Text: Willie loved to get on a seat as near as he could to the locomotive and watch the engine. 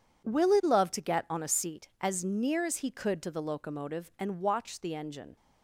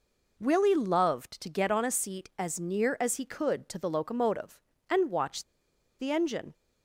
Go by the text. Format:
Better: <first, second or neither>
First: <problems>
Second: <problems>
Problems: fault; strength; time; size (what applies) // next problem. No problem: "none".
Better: first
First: none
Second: pauses between "watch" and "the"; noticeable; at 5.4 s; 0.56 s long